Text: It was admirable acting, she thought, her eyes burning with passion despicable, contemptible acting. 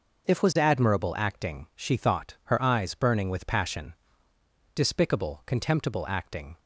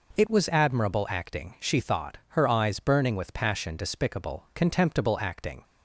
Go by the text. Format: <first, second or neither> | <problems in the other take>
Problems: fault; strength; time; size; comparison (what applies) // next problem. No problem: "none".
second | says "If" for "It"; at 0.2 s // pauses between "passion" and "despicable"; noticeable; at 3.9 s; 0.80 s long